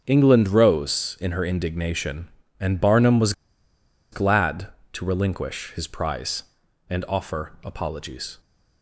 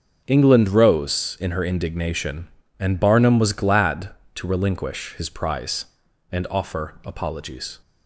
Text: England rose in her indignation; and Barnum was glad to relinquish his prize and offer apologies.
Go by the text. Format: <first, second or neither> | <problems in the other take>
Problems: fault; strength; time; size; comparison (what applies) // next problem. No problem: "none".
second | starts louder than the rest; until 1.0 s; 6.5 dB; also in the second // pauses between "was" and "glad"; noticeable; at 3.3 s; 0.79 s long